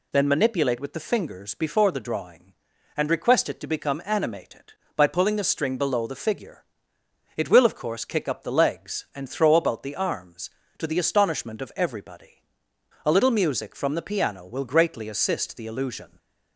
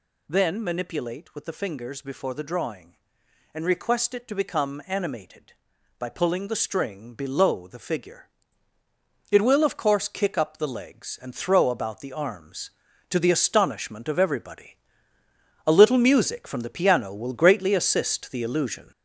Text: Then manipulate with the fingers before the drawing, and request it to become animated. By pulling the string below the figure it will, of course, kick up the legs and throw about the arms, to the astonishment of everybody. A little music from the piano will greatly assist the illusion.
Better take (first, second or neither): first